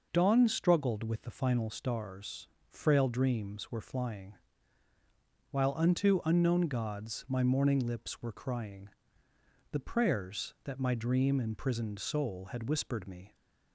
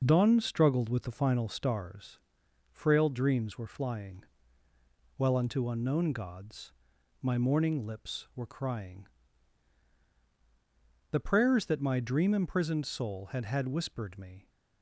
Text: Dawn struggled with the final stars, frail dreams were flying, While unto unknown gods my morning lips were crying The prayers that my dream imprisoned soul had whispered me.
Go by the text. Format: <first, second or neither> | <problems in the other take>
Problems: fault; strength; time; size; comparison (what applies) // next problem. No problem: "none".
first | pauses between "gods" and "my"; noticeable; at 6.7 s; 0.48 s long // pauses between "crying" and "The"; strong; at 9.0 s; 2.0 s long; noticeable in the first // says "had" twice; at 13.4 s